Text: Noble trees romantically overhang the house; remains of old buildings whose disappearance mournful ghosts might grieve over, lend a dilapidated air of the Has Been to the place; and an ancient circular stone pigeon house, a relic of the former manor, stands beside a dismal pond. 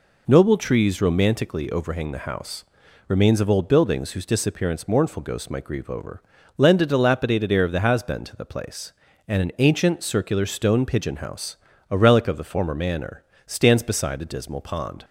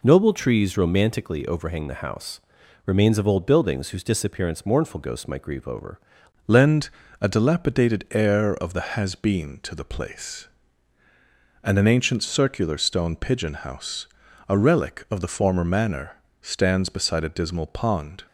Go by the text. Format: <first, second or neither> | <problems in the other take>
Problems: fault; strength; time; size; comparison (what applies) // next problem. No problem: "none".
first | changes voice at "lend"; from 6.4 s on; 11.8 s long // pauses between "lend" and "a"; slight; at 6.8 s; 0.30 s long